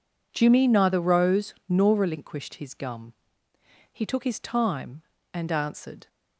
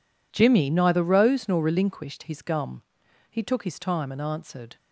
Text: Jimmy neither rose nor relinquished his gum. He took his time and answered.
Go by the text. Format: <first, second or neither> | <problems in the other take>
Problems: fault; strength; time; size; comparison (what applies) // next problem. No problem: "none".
neither | none